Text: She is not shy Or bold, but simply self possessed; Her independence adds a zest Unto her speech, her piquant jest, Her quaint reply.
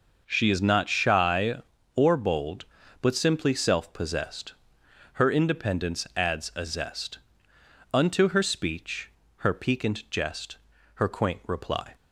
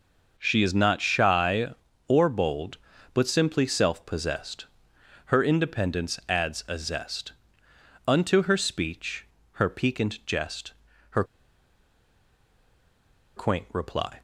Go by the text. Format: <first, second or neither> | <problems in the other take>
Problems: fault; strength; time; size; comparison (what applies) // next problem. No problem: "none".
first | pauses between "zest" and "Unto"; noticeable; at 7.3 s; 0.74 s long; noticeable in the first // pauses between "Her" and "quaint"; strong; at 11.2 s; 2.1 s long